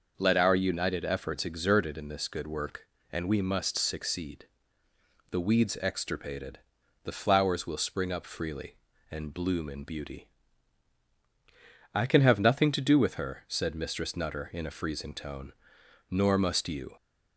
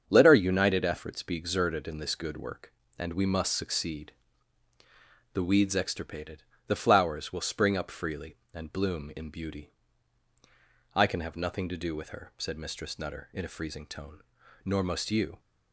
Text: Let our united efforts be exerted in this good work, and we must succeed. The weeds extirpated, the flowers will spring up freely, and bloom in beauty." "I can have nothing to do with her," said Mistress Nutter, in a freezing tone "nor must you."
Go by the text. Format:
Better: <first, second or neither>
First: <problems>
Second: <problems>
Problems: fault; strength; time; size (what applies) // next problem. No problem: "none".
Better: second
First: starts louder than the rest; noticeable; until 1.1 s; 6 dB // skips "be"; at 1.4 s // pauses between "tone" and "nor"; noticeable; at 15.5 s; 0.58 s long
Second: starts louder than the rest; strong; until 1.0 s; 7 dB // pauses between "tone" and "nor"; at 14.2 s; 0.42 s long